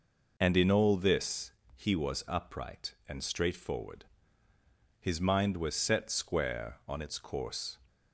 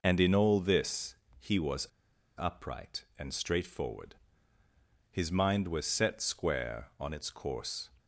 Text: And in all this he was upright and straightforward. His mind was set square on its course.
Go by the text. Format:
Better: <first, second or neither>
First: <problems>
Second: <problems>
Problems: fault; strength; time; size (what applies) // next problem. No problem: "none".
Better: first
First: pauses between "this" and "he"; slight; at 1.5 s; 0.24 s long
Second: pauses between "this" and "he"; slight; at 1.1 s; 0.24 s long // pauses between "was" and "upright"; noticeable; at 1.8 s; 0.48 s long